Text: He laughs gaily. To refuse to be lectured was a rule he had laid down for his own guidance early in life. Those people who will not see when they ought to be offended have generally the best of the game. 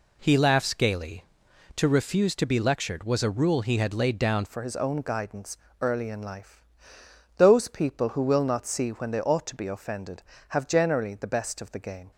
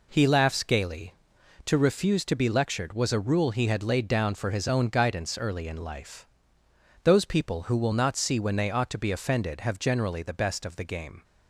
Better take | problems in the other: second | changes voice at "for"; from 4.4 s on; 7.7 s long // pauses between "guidance" and "early"; slight; at 5.5 s; 0.24 s long

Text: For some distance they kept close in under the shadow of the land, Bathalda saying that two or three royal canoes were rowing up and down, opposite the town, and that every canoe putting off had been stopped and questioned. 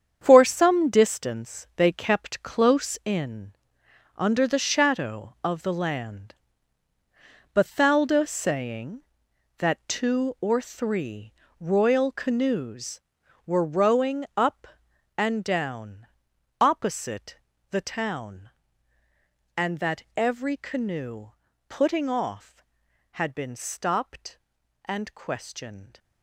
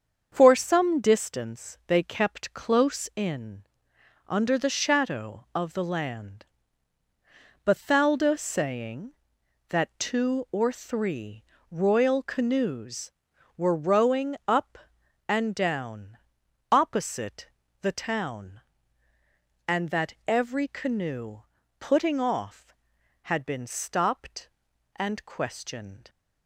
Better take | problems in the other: second | gets quieter; strong; throughout; 10 dB // starts louder than the rest; strong; until 1.2 s; 8 dB; also in the second // pauses between "in" and "under"; noticeable; at 3.5 s; 0.62 s long; noticeable in the second // pauses between "three" and "royal"; slight; at 11.3 s; 0.26 s long; slight in the second // pauses between "opposite" and "the"; slight; at 17.3 s; 0.32 s long; slight in the second // pauses between "canoe" and "putting"; at 21.3 s; 0.38 s long; also in the second

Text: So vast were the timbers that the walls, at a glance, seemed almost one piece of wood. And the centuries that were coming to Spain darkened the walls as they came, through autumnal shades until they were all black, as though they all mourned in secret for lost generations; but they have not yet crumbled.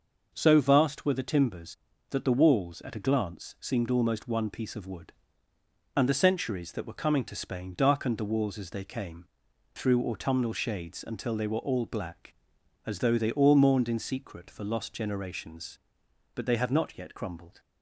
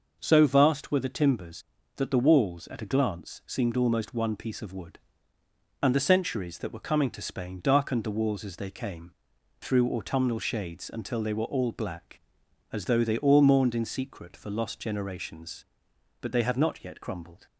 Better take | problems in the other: neither | none

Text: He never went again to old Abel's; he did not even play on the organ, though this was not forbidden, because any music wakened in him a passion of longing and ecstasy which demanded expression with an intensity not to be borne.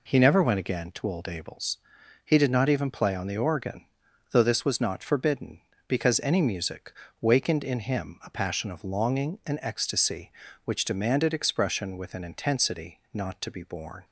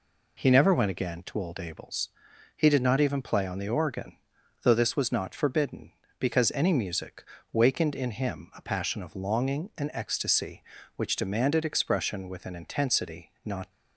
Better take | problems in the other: first | pauses between "music" and "wakened"; slight; at 7.2 s; 0.28 s long; slight in the first // stops before "to be borne"; at 13.7 s

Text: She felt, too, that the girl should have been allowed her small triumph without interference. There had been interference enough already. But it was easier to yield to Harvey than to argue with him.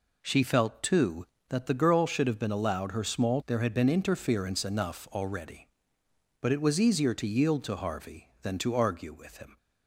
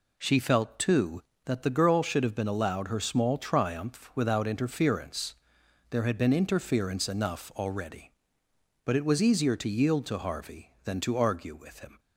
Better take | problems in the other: second | skips "triumph without interference"; at 3.4 s

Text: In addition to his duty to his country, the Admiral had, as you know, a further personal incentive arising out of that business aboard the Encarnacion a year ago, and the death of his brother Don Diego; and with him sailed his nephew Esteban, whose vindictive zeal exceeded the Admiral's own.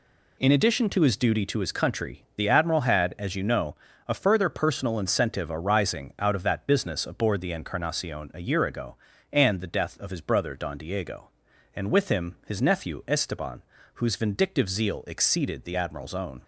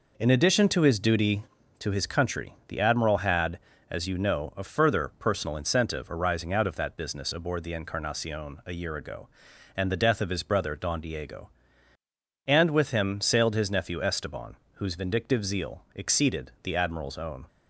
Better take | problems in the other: second | skips "sailed"; at 12.4 s

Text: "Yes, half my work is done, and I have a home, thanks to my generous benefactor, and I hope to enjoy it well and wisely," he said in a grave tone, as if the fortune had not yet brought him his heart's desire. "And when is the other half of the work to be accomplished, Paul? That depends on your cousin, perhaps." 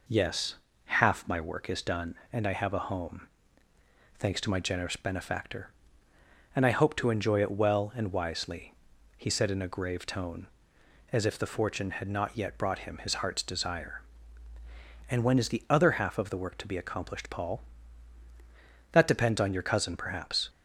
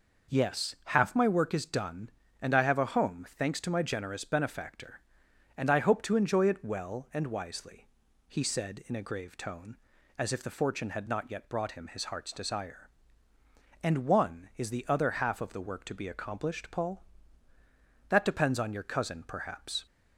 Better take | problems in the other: first | says "one" for "when"; at 14.0 s

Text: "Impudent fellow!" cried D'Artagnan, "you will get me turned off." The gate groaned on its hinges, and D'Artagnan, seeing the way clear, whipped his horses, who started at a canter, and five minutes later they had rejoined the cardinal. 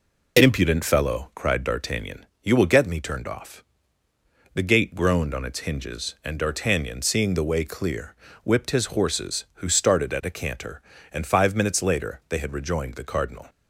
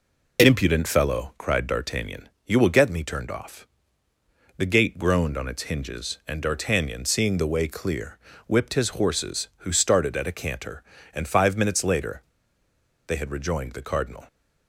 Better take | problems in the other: first | pauses between "later" and "they"; noticeable; at 12.2 s; 0.84 s long

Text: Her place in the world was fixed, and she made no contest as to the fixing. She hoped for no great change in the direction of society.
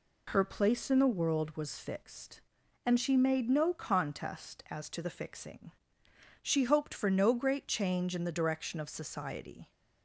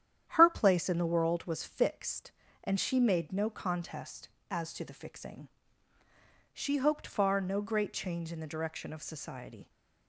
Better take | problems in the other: first | starts louder than the rest; strong; until 1.2 s; 10 dB // says "far" for "for"; at 7.0 s

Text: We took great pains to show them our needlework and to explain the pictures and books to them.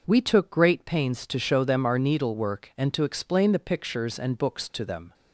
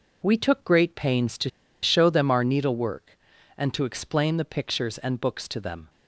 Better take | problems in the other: first | pauses between "to" and "show"; slight; at 1.4 s; 0.33 s long

